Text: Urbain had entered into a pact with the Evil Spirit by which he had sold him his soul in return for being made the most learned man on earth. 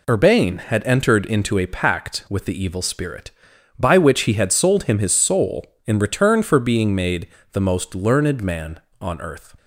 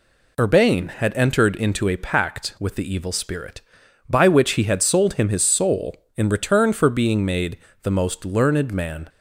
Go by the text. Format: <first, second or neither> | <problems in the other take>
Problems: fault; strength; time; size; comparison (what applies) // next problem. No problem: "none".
first | pauses between "made" and "the"; slight; at 7.5 s; 0.26 s long; slight in the first // stops before "on earth"; at 9.0 s